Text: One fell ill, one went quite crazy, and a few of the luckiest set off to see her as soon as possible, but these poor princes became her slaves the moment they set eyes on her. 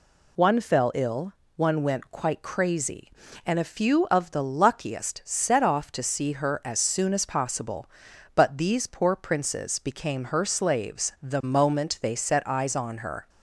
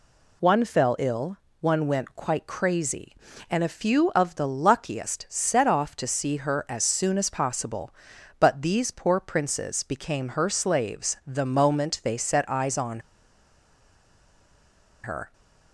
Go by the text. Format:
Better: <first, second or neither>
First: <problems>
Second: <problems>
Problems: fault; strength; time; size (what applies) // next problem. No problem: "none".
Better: first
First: none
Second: pauses between "on" and "her"; strong; at 13.0 s; 2.0 s long